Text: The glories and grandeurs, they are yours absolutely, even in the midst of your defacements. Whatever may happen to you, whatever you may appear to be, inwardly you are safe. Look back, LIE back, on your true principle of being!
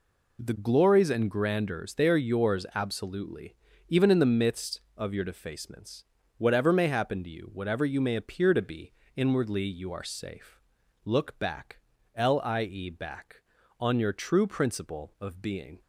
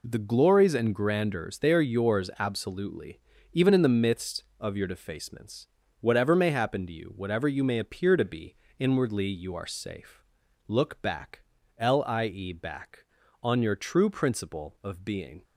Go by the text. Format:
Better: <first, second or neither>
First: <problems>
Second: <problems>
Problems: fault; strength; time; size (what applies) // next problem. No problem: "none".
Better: neither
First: none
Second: none